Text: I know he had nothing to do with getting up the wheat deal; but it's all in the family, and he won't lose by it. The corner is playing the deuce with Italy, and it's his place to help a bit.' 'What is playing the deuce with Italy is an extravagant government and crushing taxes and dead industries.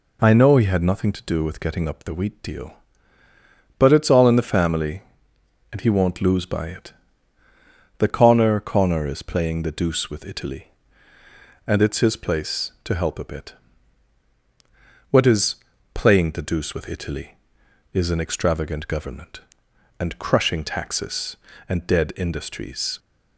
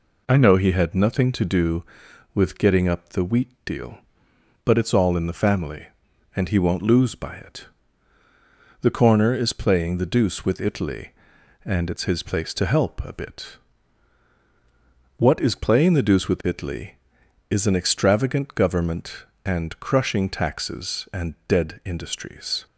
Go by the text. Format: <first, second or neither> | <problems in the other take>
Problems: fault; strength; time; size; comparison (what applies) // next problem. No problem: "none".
second | says "corner" twice; at 8.6 s // pauses between "is" and "playing"; at 15.5 s; 0.40 s long